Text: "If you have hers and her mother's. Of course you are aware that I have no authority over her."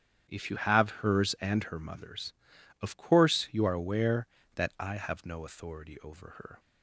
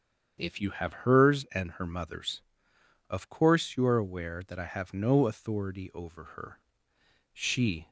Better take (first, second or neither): first